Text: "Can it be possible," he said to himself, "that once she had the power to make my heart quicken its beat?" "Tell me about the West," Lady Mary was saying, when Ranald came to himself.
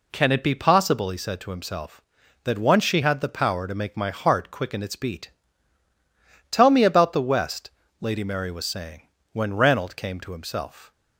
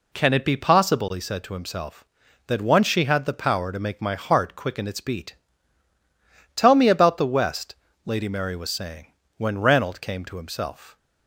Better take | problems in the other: neither | none

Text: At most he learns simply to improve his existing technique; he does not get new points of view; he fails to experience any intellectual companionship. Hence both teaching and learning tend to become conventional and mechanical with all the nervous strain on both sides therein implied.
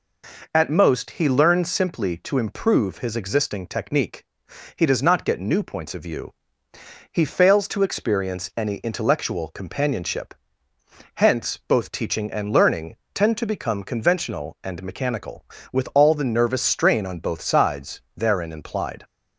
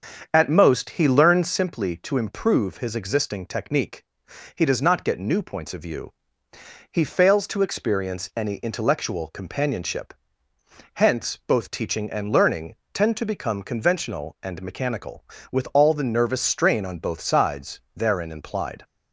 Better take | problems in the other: first | starts louder than the rest; strong; until 1.5 s; 7 dB // pauses between "learning" and "tend"; slight; at 12.7 s; 0.16 s long; slight in the first // pauses between "sides" and "therein"; slight; at 17.7 s; 0.16 s long; slight in the first

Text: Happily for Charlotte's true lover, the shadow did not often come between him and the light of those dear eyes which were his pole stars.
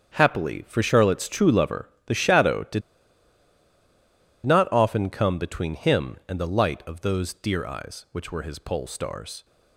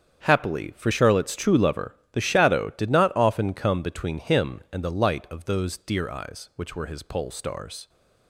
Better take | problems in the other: second | starts louder than the rest; strong; until 1.2 s; 7.5 dB; strong in the second // pauses between "did" and "not"; strong; at 2.8 s; 1.6 s long

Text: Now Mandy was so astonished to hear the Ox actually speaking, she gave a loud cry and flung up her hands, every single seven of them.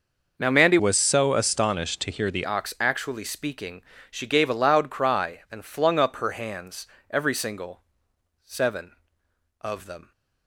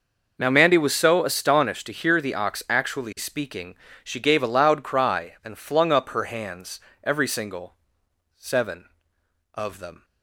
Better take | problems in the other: second | changes voice from "was" to "the"; from 0.7 to 2.4 s; 1.7 s long // pauses between "single" and "seven"; noticeable; at 7.8 s; 0.62 s long; noticeable in the second

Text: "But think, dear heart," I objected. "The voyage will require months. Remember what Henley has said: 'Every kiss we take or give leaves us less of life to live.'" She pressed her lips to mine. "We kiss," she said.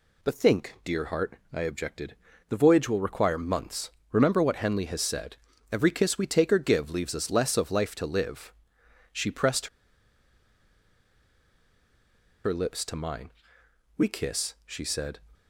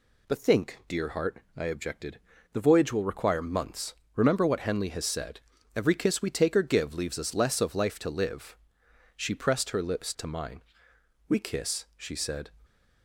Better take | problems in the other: second | pauses between "pressed" and "her"; strong; at 9.6 s; 2.7 s long

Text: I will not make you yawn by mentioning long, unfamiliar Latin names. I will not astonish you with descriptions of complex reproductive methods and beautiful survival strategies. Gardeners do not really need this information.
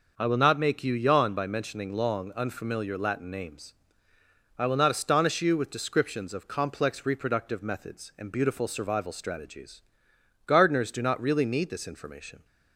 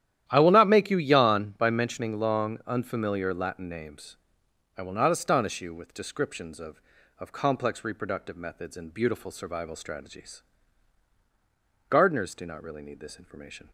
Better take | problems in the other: first | starts louder than the rest; strong; until 1.2 s; 11.5 dB // says "of" twice; at 7.1 s

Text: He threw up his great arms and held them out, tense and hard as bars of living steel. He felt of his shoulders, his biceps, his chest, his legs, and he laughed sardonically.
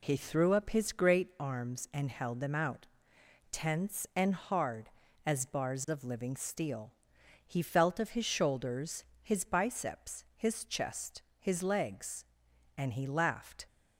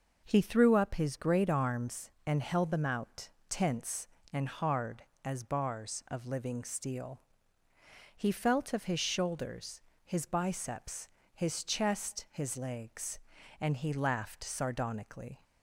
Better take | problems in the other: second | stops before "sardonically"; at 13.6 s

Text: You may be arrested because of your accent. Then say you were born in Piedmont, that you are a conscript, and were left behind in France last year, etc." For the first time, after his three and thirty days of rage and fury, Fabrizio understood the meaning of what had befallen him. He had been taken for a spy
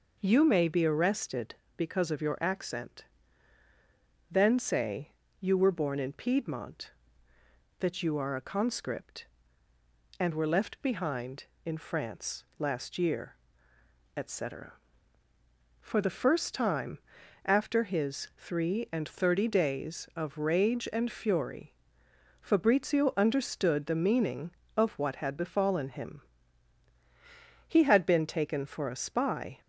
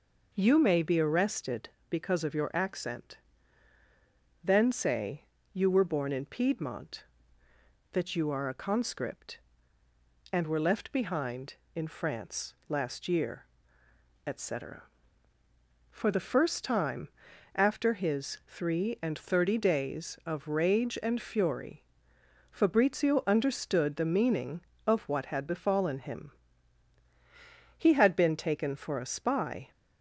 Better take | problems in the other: neither | pauses between "say" and "you"; slight; the same in both

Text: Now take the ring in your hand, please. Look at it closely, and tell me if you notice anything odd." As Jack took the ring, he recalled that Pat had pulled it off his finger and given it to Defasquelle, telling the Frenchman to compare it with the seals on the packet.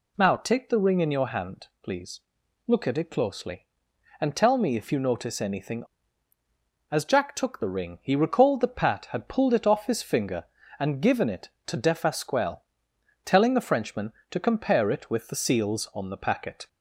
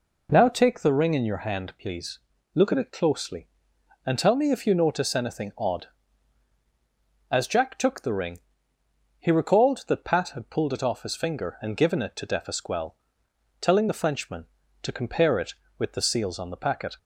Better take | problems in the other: second | skips "odd"; at 6.3 s

